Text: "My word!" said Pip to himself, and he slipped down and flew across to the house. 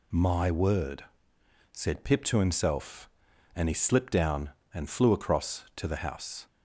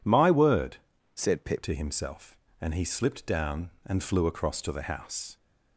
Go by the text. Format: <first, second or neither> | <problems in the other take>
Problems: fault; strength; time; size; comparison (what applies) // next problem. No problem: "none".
first | changes voice from "said" to "Pip"; from 1.1 to 1.6 s; 0.5 s long